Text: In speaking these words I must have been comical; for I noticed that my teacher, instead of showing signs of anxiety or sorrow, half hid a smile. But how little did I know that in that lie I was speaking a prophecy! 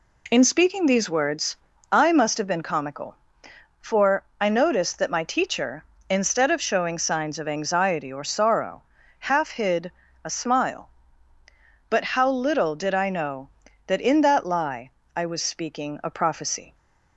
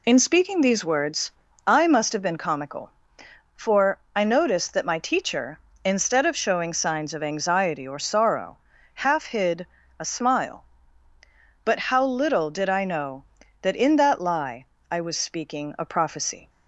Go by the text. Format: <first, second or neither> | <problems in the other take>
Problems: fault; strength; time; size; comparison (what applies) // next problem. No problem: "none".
first | loses the start of "In"; at 0.0 s; 35 ms // pauses between "words" and "I"; slight; at 1.2 s; 0.34 s long; slight in the first // pauses between "for" and "I"; slight; at 3.9 s; 0.16 s long; slight in the first // pauses between "hid" and "a"; slight; at 9.6 s; 0.32 s long; slight in the first // pauses between "lie" and "I"; slight; at 14.6 s; 0.24 s long; slight in the first